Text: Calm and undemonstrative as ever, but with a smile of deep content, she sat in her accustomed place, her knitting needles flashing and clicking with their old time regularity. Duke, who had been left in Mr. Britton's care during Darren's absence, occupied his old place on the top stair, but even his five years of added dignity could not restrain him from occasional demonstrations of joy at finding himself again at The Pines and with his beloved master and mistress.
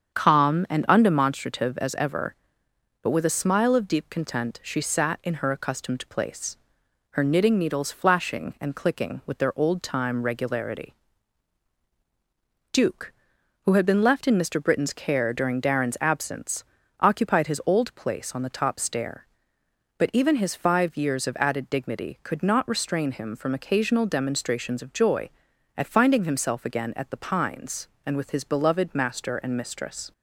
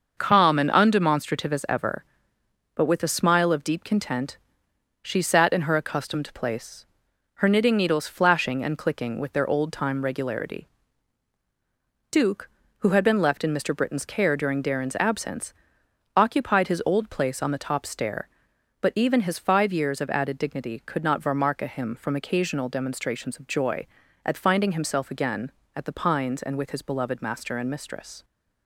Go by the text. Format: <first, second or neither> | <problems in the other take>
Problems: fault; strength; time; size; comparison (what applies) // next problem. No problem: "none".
first | starts louder than the rest; until 1.1 s; 6.5 dB; strong in the first // says "varmarka" for "restrain"; at 21.2 s